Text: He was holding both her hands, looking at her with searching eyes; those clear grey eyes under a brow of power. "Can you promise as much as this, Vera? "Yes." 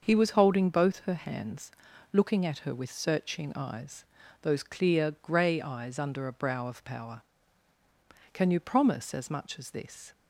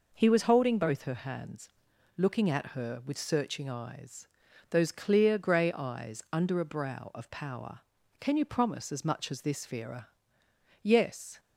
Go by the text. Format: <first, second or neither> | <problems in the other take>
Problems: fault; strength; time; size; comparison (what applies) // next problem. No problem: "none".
second | starts louder than the rest; until 1.1 s; 6.5 dB // stops before "Vera Yes"; at 10.1 s